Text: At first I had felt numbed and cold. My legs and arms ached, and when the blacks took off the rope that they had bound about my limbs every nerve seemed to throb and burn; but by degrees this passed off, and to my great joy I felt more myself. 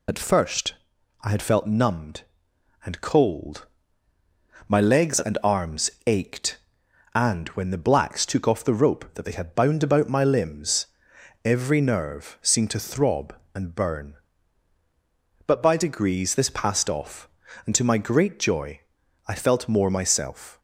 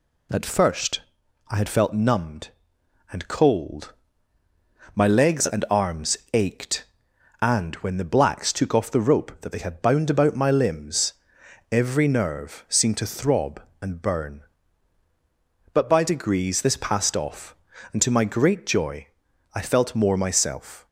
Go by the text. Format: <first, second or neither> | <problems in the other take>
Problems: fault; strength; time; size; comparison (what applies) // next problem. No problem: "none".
second | loses the start of "At"; at 0.0 s; 50 ms // pauses between "first" and "I"; noticeable; at 0.7 s; 0.48 s long; noticeable in the second // pauses between "arms" and "ached"; slight; at 5.8 s; 0.16 s long; slight in the second // pauses between "limbs" and "every"; noticeable; at 10.8 s; 0.58 s long; noticeable in the second // pauses between "joy" and "I"; at 18.8 s; 0.44 s long; also in the second